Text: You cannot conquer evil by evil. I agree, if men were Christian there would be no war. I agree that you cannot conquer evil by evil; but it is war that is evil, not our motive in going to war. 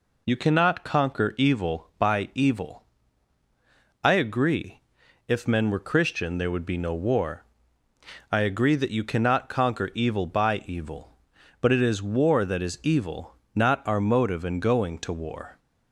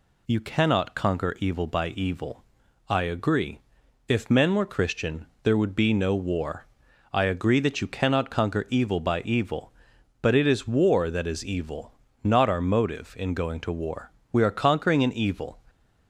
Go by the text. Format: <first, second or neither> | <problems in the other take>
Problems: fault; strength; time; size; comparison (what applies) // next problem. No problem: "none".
first | pauses between "Christian" and "there"; slight; at 5.2 s; 0.16 s long // goes on to say "We are conquering an evil"; noticeable; from 14.3 s on; 1.2 s long